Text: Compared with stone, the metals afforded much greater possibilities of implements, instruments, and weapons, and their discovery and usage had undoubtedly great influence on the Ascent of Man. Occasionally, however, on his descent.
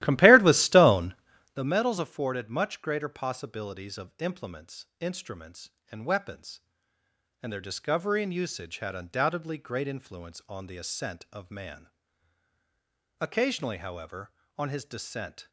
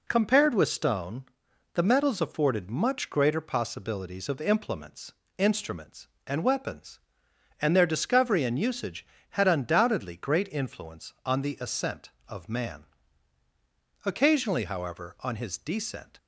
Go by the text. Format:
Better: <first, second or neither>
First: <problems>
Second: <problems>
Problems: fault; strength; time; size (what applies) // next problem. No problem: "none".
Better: second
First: starts louder than the rest; strong; until 1.6 s; 15.5 dB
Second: none